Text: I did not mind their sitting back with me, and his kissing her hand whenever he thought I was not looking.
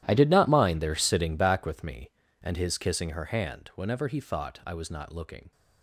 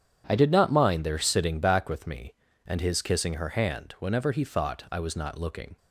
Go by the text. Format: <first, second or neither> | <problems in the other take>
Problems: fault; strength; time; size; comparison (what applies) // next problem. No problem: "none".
second | gets quieter; strong; throughout; 17.5 dB // starts louder than the rest; strong; until 1.0 s; 12.5 dB; strong in the second